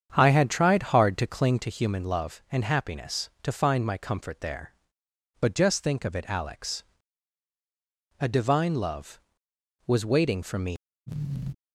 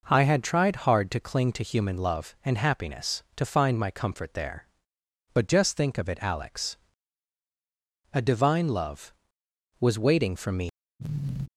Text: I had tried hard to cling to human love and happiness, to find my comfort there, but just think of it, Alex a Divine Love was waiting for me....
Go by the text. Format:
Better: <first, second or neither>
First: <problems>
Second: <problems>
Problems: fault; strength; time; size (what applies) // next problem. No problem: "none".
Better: second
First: starts louder than the rest; strong; until 1.7 s; 8 dB // pauses between "Alex" and "a"; strong; at 6.8 s; 1.3 s long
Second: pauses between "Alex" and "a"; strong; at 6.7 s; 1.3 s long